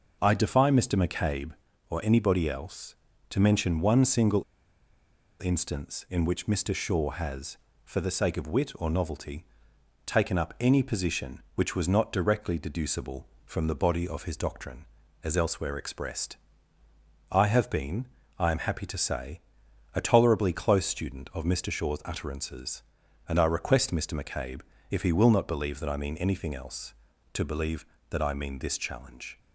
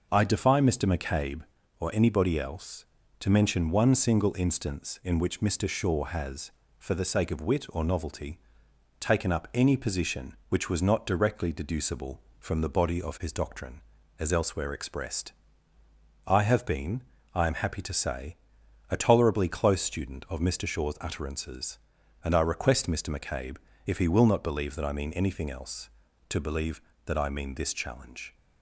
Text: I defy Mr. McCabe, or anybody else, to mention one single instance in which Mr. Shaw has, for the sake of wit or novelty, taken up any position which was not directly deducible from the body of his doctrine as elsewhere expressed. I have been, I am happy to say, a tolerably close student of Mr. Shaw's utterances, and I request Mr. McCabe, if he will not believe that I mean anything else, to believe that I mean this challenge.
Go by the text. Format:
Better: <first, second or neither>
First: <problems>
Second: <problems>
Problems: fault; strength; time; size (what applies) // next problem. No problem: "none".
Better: second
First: pauses between "single" and "instance"; at 4.4 s; 1.0 s long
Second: none